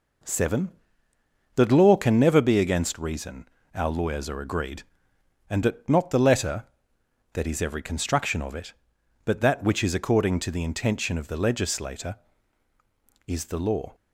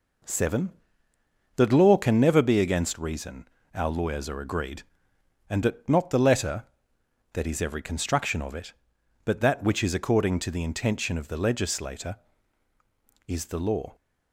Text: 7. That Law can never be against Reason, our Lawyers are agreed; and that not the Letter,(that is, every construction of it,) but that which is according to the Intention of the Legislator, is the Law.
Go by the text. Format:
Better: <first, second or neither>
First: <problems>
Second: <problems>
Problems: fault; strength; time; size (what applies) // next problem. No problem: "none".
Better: neither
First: none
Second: none